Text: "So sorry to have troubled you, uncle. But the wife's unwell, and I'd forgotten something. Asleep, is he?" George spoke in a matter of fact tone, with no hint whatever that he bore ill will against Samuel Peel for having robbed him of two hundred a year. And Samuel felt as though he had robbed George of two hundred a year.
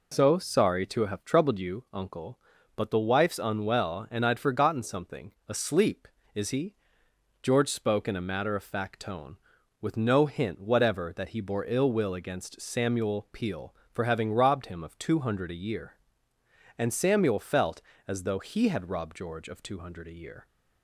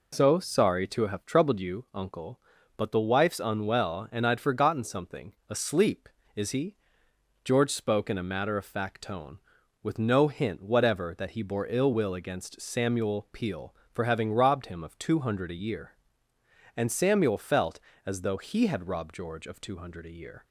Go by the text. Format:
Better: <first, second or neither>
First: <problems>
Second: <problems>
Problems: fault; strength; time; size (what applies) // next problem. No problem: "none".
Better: neither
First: none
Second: none